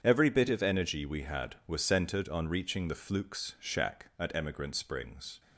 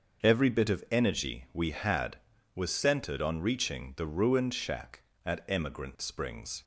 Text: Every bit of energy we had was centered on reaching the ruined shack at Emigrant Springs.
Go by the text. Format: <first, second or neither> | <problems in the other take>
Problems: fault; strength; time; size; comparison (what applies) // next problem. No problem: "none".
second | starts louder than the rest; strong; until 1.0 s; 7.5 dB; also in the second // says "flukes" for "ruined"; at 2.9 s